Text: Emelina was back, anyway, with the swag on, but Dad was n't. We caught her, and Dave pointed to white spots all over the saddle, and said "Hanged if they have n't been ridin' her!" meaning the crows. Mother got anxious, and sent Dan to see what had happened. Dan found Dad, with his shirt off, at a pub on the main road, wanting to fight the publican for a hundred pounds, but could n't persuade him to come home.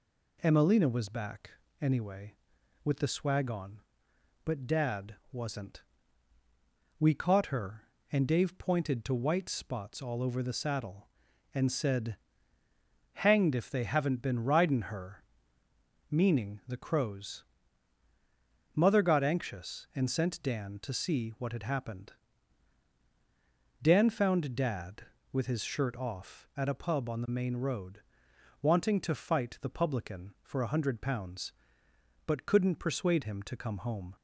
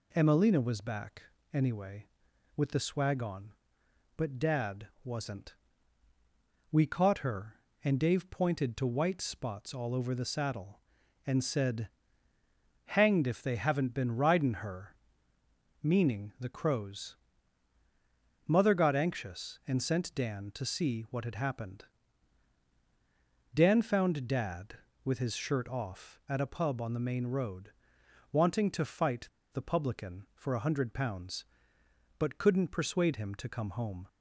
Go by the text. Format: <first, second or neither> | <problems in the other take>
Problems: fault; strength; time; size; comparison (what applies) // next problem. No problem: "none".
first | pauses between "said" and "Hanged"; noticeable; at 11.8 s; 0.98 s long; noticeable in the first // pauses between "fight" and "the"; slight; at 29.2 s; 0.26 s long